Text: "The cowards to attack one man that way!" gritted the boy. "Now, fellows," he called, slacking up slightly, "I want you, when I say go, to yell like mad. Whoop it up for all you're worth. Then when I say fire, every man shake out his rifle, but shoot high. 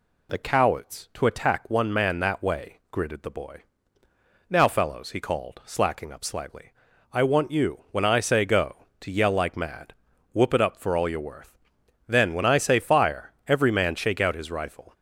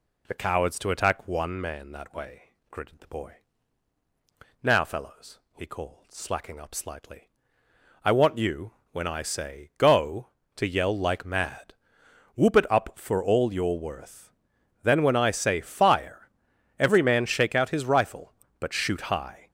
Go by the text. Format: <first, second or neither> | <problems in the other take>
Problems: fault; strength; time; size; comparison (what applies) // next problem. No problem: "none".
second | stops before "but shoot high"; at 14.9 s